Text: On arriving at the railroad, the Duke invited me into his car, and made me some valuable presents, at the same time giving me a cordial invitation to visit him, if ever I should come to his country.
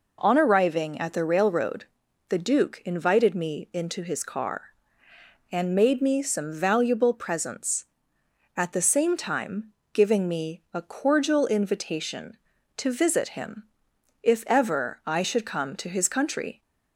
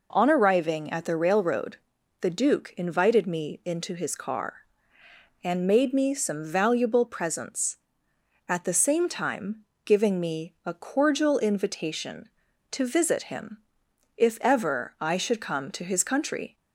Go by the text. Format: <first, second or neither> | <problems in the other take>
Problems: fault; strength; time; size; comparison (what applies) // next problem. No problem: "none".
neither | pauses between "time" and "giving"; slight; the same in both